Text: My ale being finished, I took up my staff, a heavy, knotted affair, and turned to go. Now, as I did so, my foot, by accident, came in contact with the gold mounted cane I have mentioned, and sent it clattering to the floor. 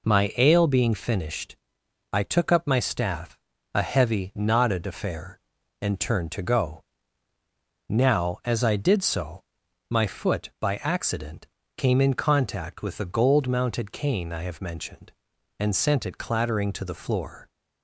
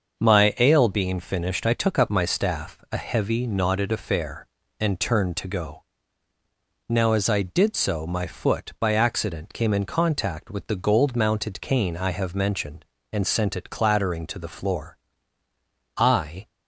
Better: first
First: none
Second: starts louder than the rest; until 1.2 s; 6.5 dB // goes on to say "I"; from 15.9 s on; 0.50 s long

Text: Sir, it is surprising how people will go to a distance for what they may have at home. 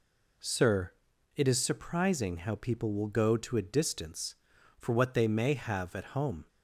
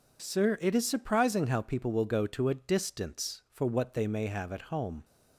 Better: neither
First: none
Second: none

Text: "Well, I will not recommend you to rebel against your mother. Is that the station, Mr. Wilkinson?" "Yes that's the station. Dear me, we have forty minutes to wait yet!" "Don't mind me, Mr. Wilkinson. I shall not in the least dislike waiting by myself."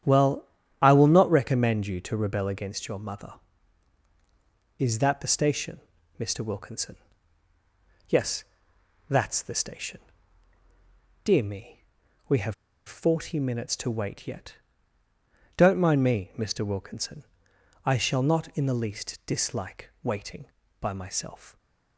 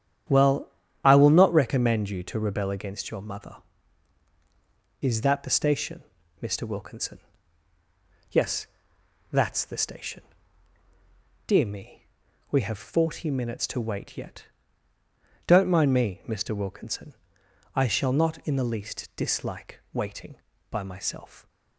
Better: second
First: starts louder than the rest; strong; until 1.3 s; 9.5 dB // pauses between "Yes" and "that's"; noticeable; at 8.4 s; 0.66 s long // pauses between "have" and "forty"; slight; at 12.5 s; 0.33 s long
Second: starts louder than the rest; strong; until 1.6 s; 9.5 dB // pauses between "Yes" and "that's"; noticeable; at 8.6 s; 0.66 s long

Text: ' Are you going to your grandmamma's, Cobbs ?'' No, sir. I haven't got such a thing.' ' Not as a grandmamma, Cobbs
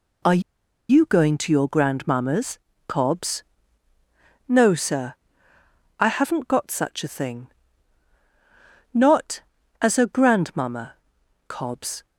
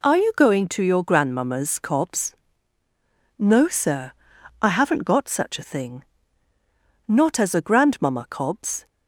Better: second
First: pauses between "Are" and "you"; noticeable; at 0.4 s; 0.50 s long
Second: none

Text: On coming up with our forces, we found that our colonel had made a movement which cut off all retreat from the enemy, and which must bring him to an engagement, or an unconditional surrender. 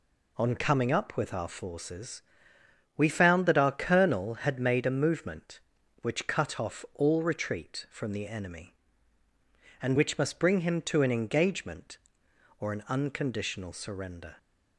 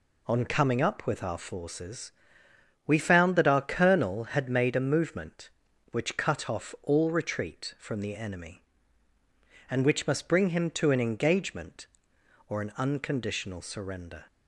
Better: neither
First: none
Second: none

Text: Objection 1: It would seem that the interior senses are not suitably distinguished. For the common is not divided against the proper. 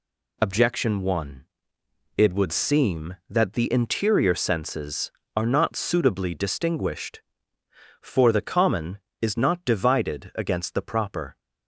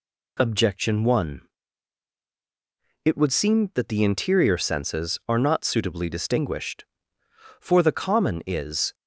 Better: first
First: none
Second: stops before "not divided against the proper"; at 8.9 s

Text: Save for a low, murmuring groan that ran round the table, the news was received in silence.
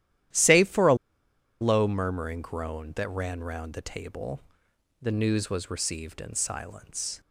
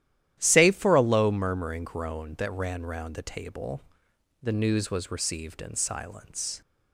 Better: second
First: starts louder than the rest; strong; until 1.9 s; 12 dB // pauses between "a" and "low"; noticeable; at 0.9 s; 0.66 s long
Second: starts louder than the rest; strong; until 1.4 s; 12 dB

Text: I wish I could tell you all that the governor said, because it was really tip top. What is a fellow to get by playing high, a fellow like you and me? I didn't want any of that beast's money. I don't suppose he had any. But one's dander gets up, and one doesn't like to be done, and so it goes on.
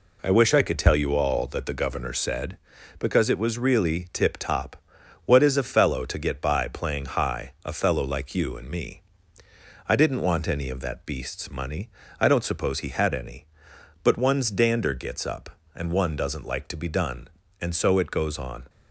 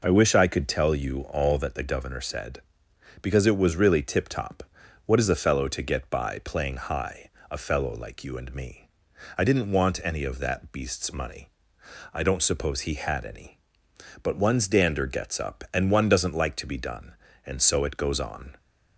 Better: neither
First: none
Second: none

